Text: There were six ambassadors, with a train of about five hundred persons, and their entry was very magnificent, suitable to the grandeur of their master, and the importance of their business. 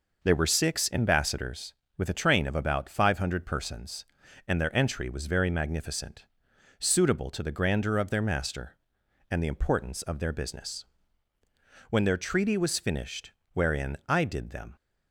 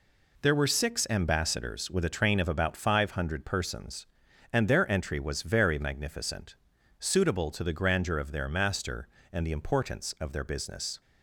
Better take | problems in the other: second | goes on to say "When their treaty was finished wherein I did them"; strong; from 11.8 s on; 2.8 s long

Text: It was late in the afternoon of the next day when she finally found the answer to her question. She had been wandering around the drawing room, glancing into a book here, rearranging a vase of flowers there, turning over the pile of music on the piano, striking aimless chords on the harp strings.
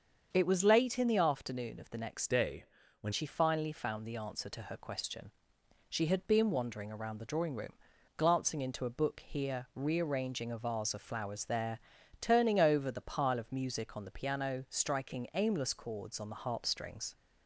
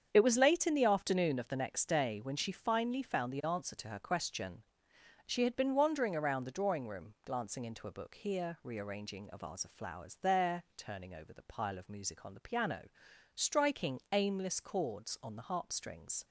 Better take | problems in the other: second | starts louder than the rest; strong; until 1.3 s; 7 dB; strong in the second // changes voice from "day" to "when"; from 2.2 to 3.1 s; 0.9 s long // pauses between "day" and "when"; slight; at 2.6 s; 0.36 s long

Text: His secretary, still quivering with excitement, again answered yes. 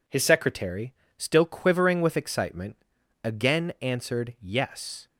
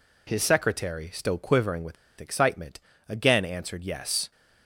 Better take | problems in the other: first | pauses between "with" and "excitement"; slight; at 1.9 s; 0.25 s long

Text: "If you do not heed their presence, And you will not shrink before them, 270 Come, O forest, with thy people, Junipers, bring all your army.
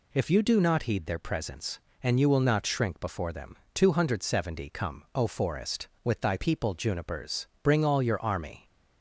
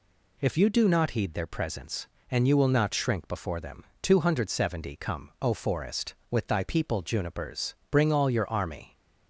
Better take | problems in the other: neither | none

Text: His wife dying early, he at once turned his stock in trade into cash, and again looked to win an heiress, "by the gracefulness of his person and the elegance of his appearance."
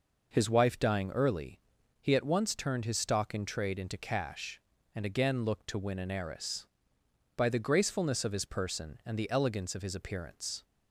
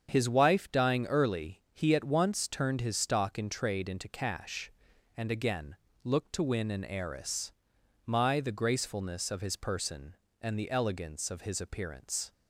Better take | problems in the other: first | starts louder than the rest; strong; until 1.1 s; 7.5 dB // pauses between "again" and "looked"; slight; at 5.7 s; 0.28 s long // says "my" for "by"; at 8.0 s

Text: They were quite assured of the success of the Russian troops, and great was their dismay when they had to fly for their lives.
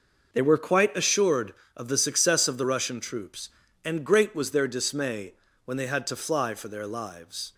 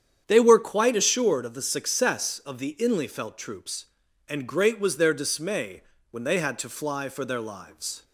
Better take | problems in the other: first | starts louder than the rest; strong; until 1.2 s; 8.5 dB; noticeable in the first // says "Inlyfelt" for "Russian"; at 2.7 s // pauses between "dismay" and "when"; slight; at 5.8 s; 0.30 s long; slight in the first

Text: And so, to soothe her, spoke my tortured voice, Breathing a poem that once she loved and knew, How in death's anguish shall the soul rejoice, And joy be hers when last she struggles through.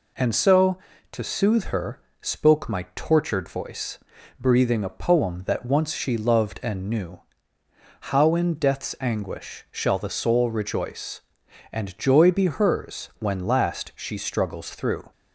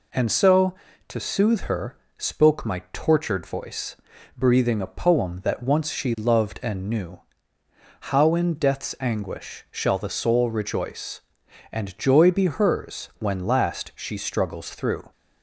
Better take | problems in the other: neither | none

